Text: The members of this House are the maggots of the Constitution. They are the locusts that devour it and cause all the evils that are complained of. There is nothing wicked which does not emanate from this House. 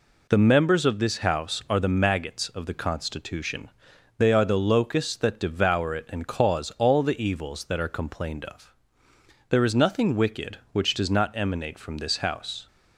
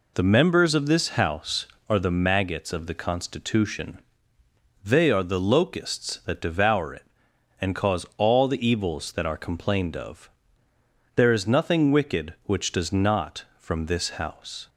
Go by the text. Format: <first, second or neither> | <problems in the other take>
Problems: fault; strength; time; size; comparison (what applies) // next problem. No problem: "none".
first | skips "emanate"; at 13.5 s